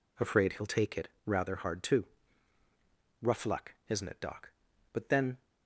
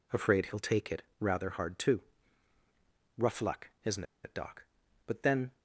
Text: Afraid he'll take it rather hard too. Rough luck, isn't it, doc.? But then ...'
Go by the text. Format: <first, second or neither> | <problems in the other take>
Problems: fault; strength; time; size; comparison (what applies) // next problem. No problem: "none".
first | pauses between "it" and "rather"; slight; at 1.0 s; 0.16 s long; slight in the first // pauses between "isn't" and "it"; slight; at 4.0 s; 0.20 s long